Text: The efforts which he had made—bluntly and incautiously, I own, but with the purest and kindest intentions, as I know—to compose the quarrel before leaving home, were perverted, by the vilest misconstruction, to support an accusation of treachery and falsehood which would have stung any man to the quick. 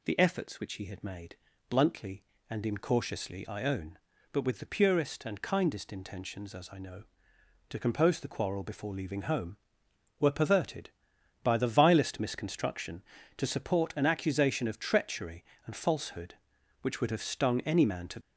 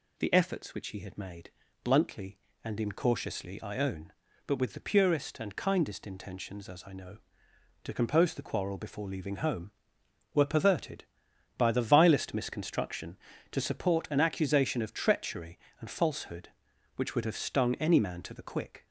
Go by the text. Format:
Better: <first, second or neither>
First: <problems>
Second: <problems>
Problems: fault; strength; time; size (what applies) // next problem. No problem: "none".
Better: second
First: stops before "the quick"; at 18.2 s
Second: none